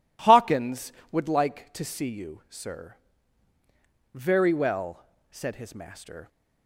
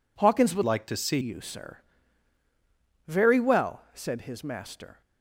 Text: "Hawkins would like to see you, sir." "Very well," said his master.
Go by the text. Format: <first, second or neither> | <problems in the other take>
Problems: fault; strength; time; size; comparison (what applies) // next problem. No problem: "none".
first | changes voice from "like" to "see"; from 0.6 to 1.1 s; 0.5 s long